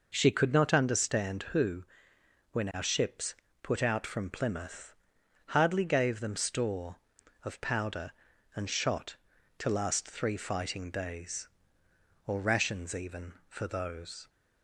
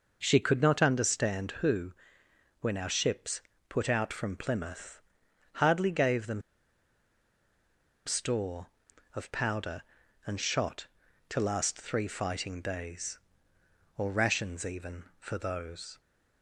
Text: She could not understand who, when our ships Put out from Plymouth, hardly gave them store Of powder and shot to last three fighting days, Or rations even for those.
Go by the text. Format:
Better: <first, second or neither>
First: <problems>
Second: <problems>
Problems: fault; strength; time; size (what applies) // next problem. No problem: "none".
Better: first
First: pauses between "ships" and "Put"; slight; at 3.3 s; 0.28 s long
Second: pauses between "ships" and "Put"; slight; at 3.4 s; 0.28 s long // pauses between "them" and "store"; strong; at 6.4 s; 1.6 s long